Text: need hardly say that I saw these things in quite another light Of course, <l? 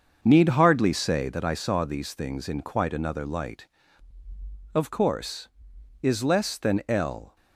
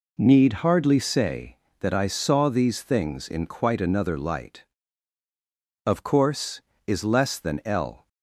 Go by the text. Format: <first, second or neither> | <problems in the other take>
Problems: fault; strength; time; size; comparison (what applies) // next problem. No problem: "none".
second | starts louder than the rest; until 1.6 s; 6.5 dB